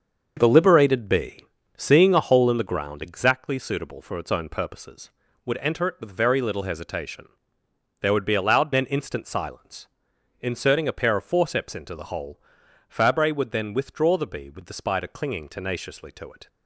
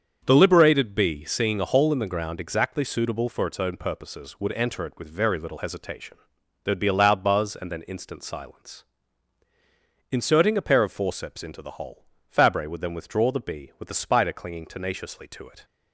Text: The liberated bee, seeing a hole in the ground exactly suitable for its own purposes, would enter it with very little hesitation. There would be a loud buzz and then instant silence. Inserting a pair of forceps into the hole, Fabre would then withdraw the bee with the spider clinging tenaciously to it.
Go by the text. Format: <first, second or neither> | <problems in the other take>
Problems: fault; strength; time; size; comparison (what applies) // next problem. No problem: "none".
second | starts louder than the rest; until 1.3 s; 6.5 dB; strong in the second // skips "buzz and"; at 8.7 s